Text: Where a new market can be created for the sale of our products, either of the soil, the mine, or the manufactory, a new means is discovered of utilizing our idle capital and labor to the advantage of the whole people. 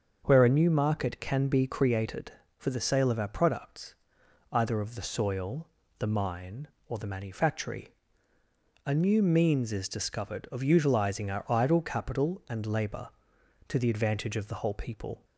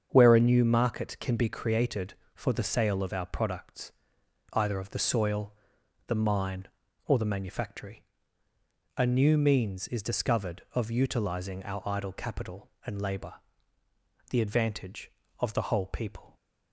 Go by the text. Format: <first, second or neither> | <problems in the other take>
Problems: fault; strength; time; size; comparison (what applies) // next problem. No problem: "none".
first | starts louder than the rest; strong; until 1.1 s; 7 dB; also in the first // skips "to"; at 13.8 s